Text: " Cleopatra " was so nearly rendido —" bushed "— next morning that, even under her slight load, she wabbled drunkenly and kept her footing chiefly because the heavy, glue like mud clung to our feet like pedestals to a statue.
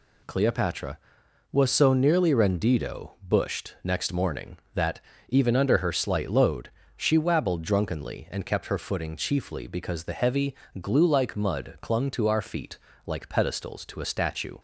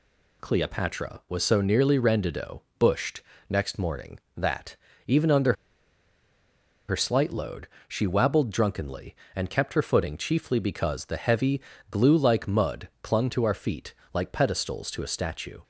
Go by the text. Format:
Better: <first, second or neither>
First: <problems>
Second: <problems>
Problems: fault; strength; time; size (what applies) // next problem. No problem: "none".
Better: first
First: pauses between "feet" and "like"; slight; at 12.7 s; 0.26 s long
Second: pauses between "under" and "her"; strong; at 5.5 s; 1.3 s long // pauses between "feet" and "like"; slight; at 13.9 s; 0.20 s long